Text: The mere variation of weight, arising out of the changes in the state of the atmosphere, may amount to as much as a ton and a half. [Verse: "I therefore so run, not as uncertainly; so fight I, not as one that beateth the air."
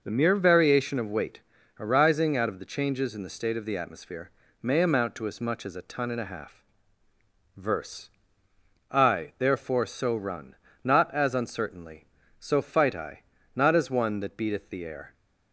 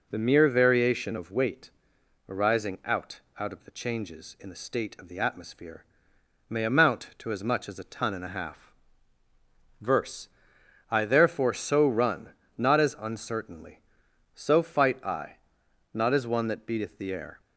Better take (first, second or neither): first